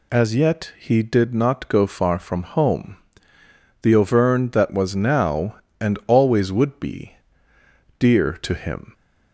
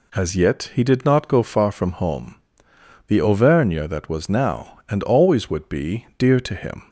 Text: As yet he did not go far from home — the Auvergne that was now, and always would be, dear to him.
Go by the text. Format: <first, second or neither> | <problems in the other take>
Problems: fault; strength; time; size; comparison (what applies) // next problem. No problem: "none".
neither | none